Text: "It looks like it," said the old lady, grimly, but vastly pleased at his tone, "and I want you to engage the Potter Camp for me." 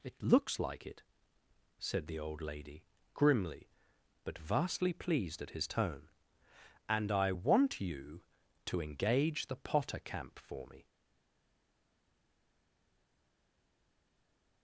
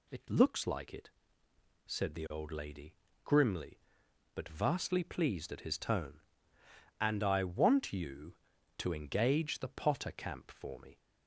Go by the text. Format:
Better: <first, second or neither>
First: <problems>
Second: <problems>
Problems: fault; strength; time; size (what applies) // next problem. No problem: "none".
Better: second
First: stays silent after the last word; strong; from 10.8 s on; 3.8 s long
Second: none